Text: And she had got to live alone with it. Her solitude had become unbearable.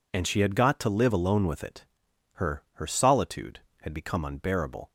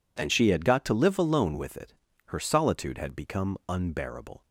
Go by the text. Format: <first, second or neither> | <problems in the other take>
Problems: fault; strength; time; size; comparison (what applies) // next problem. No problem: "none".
second | says "Her" twice; at 2.7 s